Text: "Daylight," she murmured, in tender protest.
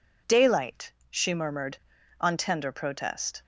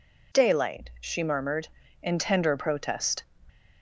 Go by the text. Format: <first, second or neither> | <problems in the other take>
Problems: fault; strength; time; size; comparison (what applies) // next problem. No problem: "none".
second | says "on" for "in"; at 2.1 s